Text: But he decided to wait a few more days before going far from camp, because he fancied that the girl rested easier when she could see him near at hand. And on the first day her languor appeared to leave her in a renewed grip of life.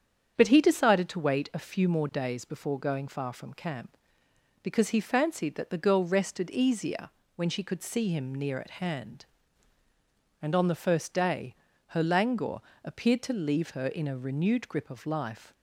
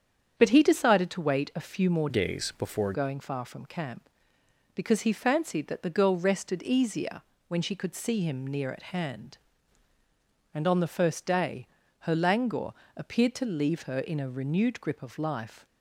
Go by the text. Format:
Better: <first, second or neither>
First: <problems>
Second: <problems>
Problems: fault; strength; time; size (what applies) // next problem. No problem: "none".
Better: first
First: starts louder than the rest; strong; until 1.3 s; 8 dB // pauses between "easier" and "when"; slight; at 7.0 s; 0.28 s long // pauses between "day" and "her"; slight; at 11.5 s; 0.36 s long // pauses between "languor" and "appeared"; slight; at 12.6 s; 0.24 s long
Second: starts louder than the rest; strong; until 1.3 s; 8 dB // changes voice from "days" to "before"; from 2.0 to 2.9 s; 0.9 s long // pauses between "easier" and "when"; slight; at 7.2 s; 0.28 s long // pauses between "day" and "her"; slight; at 11.6 s; 0.36 s long // pauses between "languor" and "appeared"; slight; at 12.7 s; 0.24 s long